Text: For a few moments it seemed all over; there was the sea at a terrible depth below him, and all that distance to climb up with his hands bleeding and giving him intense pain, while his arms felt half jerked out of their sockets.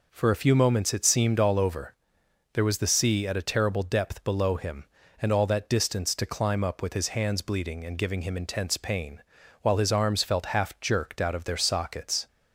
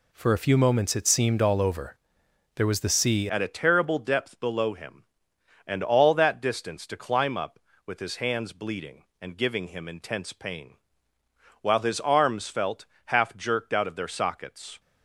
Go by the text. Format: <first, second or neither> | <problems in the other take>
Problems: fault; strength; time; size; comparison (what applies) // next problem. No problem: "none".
first | changes voice at "at"; from 3.2 s on; 11.5 s long // pauses between "felt" and "half"; slight; at 12.8 s; 0.22 s long